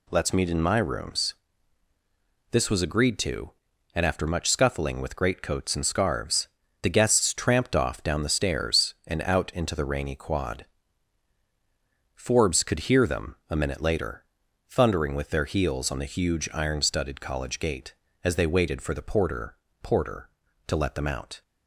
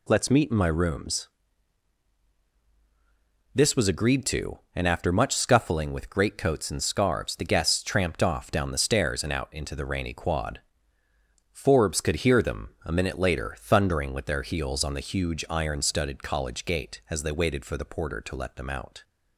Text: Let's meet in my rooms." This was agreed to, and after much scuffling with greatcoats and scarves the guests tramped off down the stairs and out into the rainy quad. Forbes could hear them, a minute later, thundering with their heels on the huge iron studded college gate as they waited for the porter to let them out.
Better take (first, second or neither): second